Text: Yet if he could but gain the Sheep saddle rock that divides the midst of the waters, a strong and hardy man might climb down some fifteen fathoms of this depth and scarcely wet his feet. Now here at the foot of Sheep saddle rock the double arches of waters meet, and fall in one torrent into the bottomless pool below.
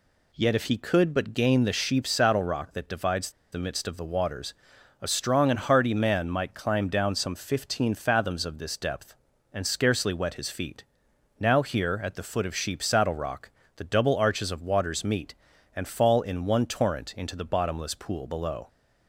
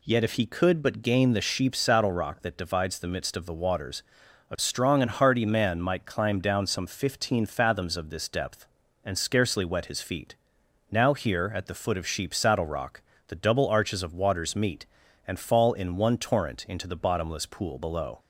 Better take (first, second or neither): second